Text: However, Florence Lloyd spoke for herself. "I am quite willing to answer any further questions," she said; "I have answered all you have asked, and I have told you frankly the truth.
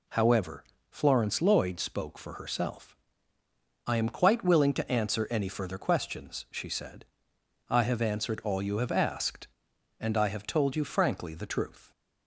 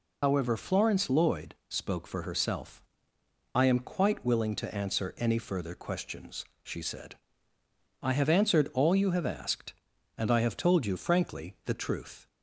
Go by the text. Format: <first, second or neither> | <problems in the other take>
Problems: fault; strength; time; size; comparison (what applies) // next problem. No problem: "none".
first | loses the start of "However"; at 0.2 s; 70 ms